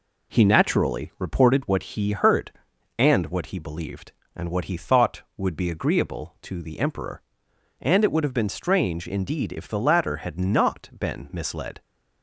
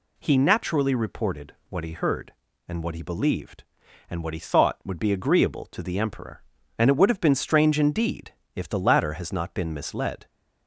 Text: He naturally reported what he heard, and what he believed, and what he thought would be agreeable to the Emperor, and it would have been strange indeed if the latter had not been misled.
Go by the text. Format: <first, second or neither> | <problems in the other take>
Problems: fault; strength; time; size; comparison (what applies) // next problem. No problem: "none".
first | pauses between "reported" and "what"; slight; at 1.5 s; 0.16 s long // pauses between "indeed" and "if"; slight; at 8.3 s; 0.22 s long // says "has" for "had"; at 9.1 s